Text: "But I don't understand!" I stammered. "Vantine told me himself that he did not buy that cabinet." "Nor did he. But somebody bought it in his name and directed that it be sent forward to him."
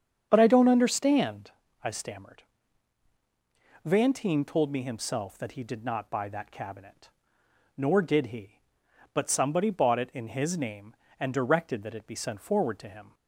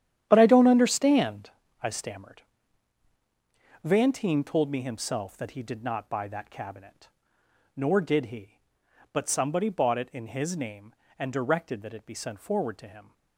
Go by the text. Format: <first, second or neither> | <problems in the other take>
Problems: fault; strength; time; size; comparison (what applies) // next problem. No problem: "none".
first | gets quieter; strong; throughout; 12 dB // starts louder than the rest; strong; until 1.2 s; 10.5 dB; strong in the first